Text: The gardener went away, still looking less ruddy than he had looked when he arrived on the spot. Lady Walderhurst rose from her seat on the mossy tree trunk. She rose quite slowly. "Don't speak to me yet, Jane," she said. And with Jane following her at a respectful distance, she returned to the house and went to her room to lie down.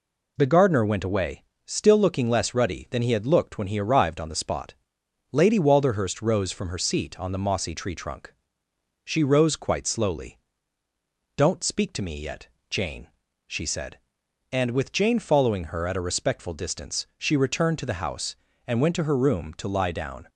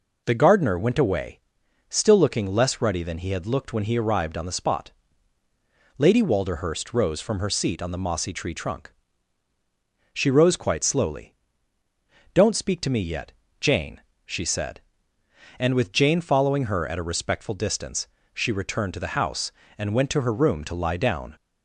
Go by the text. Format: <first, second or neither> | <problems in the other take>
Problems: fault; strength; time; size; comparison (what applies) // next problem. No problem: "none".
neither | none